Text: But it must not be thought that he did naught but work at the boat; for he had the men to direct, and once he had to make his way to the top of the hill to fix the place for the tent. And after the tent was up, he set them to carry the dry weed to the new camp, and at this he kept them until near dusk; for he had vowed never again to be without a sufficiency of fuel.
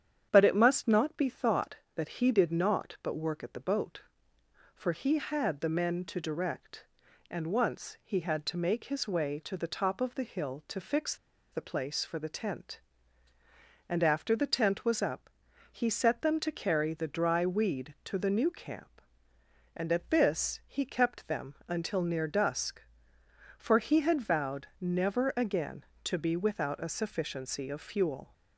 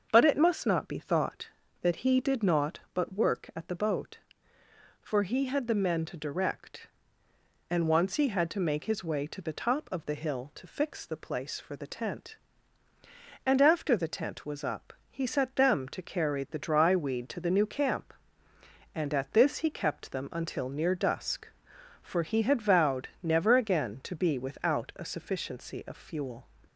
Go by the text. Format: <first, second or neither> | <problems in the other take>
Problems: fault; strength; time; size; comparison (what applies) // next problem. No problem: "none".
second | starts louder than the rest; strong; until 1.3 s; 9 dB; also in the second // pauses between "fix" and "the"; at 11.1 s; 0.36 s long